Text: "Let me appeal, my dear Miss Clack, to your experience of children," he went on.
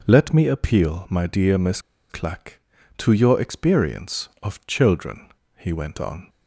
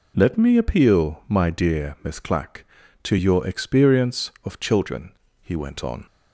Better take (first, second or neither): second